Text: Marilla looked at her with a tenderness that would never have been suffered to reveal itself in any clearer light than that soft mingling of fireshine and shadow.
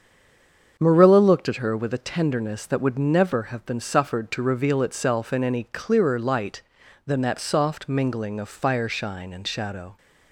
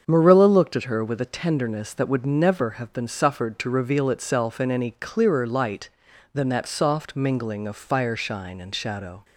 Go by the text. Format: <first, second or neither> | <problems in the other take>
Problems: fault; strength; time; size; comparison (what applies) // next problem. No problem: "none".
second | stays silent before the first word; slight; until 0.7 s; 0.7 s long // starts louder than the rest; until 1.7 s; 7 dB; also in the second